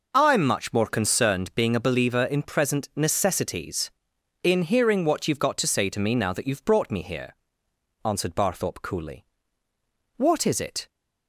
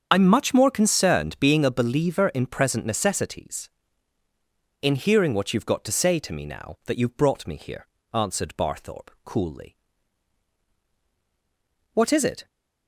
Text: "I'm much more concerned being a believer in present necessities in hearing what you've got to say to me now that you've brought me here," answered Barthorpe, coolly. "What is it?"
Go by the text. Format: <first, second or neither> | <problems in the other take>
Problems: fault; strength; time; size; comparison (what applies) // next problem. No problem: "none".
first | loses the start of "I'm"; at 0.1 s; 40 ms // starts louder than the rest; until 1.1 s; 7 dB